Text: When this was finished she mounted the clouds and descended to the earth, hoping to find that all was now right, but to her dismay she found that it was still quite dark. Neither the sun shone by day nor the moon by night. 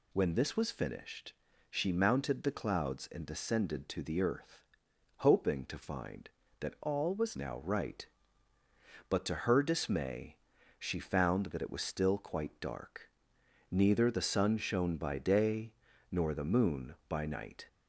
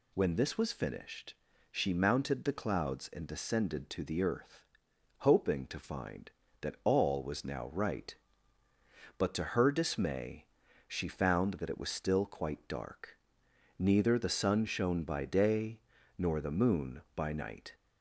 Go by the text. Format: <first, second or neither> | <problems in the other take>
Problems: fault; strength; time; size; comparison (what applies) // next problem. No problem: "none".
second | pauses between "finished" and "she"; slight; at 1.3 s; 0.36 s long; slight in the second // changes voice from "all" to "was"; from 6.8 to 7.3 s; 0.5 s long // pauses between "dismay" and "she"; at 10.3 s; 0.42 s long; also in the second // pauses between "day" and "nor"; at 15.7 s; 0.40 s long; also in the second